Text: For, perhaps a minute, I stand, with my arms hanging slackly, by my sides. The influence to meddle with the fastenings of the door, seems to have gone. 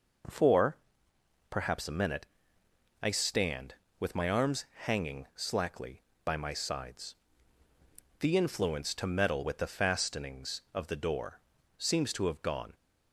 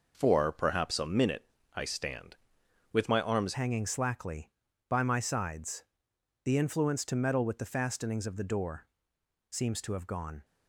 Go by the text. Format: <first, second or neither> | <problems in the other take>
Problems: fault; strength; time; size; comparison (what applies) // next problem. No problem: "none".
first | changes voice at "hanging"; from 3.5 s on; 6.9 s long